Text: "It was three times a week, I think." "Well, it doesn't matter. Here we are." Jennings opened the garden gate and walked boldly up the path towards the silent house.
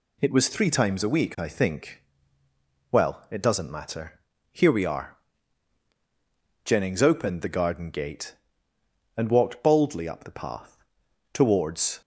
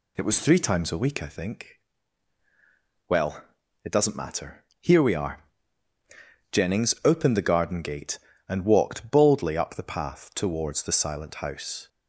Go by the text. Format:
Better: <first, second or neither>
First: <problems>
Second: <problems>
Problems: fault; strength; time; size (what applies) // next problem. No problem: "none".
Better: second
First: pauses between "path" and "towards"; noticeable; at 10.7 s; 0.56 s long // stops before "the silent house"; at 12.0 s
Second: none